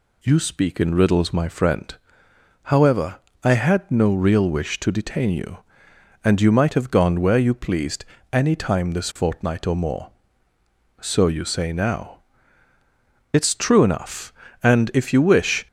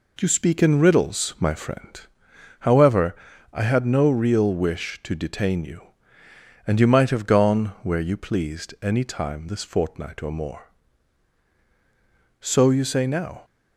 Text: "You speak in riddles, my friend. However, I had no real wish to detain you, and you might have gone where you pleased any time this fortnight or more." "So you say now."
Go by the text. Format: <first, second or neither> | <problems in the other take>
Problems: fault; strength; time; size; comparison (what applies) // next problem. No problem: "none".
second | pauses between "pleased" and "any"; slight; at 8.0 s; 0.26 s long // goes on to say "It's true enough and if you wish"; strong; from 13.3 s on; 2.3 s long